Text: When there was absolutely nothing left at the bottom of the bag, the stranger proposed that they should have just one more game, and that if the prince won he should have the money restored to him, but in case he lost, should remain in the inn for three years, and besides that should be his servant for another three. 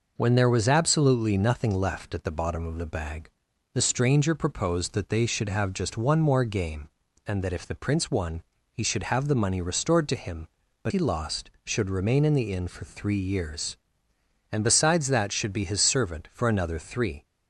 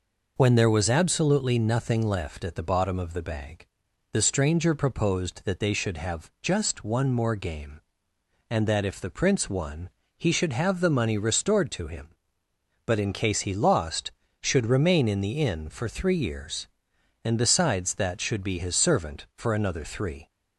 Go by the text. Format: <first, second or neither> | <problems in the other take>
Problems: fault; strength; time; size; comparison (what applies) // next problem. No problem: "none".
second | pauses between "won" and "he"; slight; at 8.4 s; 0.30 s long; slight in the second // skips "in case"; at 10.9 s